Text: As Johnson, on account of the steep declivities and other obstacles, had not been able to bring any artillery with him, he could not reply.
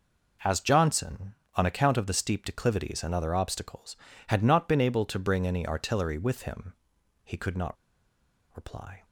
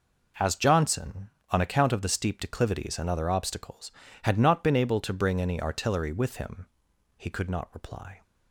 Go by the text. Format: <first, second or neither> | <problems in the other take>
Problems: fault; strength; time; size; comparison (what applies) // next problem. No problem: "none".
second | pauses between "not" and "reply"; noticeable; at 7.7 s; 0.79 s long